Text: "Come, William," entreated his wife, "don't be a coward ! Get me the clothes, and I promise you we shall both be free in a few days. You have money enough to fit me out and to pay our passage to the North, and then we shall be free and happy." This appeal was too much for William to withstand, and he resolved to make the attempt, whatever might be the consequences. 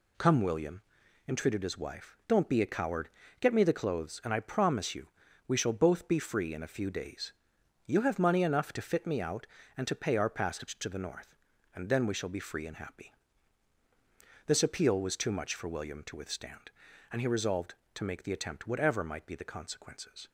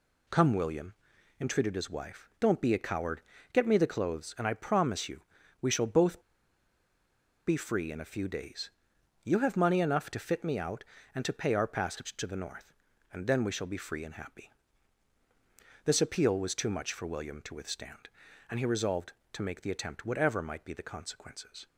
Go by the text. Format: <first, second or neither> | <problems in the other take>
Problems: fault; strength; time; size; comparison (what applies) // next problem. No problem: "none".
first | pauses between "you" and "we"; at 5.2 s; 0.38 s long; also in the first // pauses between "both" and "be"; strong; at 6.2 s; 1.2 s long